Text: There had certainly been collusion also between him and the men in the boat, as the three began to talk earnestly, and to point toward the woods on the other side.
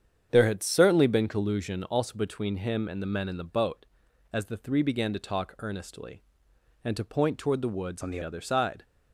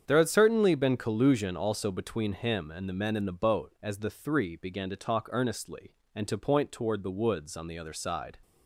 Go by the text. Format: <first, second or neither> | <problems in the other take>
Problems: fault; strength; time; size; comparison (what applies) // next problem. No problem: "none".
second | starts louder than the rest; strong; until 1.3 s; 8 dB; strong in the second // changes voice from "on" to "the"; from 8.0 to 8.1 s; 0.1 s long